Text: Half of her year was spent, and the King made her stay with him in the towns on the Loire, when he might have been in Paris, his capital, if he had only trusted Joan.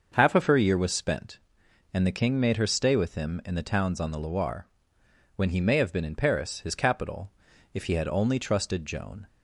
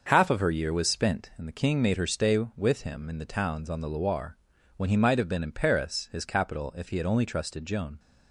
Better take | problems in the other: second | starts louder than the rest; until 1.1 s; 6.5 dB; also in the second // says "may" for "might"; at 5.6 s

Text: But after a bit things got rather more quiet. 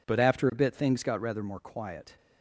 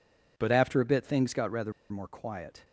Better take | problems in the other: first | pauses between "rather" and "more"; slight; at 1.7 s; 0.18 s long

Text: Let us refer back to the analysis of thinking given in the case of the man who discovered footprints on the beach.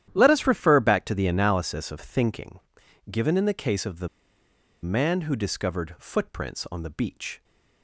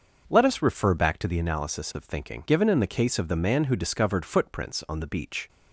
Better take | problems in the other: second | starts louder than the rest; strong; until 1.1 s; 11 dB; also in the second // pauses between "thinking" and "given"; noticeable; at 2.5 s; 0.52 s long // pauses between "the" and "man"; noticeable; at 4.0 s; 0.75 s long

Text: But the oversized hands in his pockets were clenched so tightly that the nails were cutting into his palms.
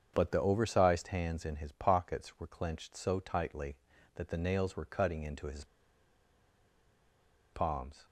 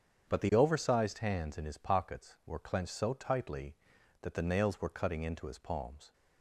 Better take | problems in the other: second | starts louder than the rest; strong; until 1.1 s; 7.5 dB; strong in the second // pauses between "his" and "palms"; strong; at 5.6 s; 1.8 s long

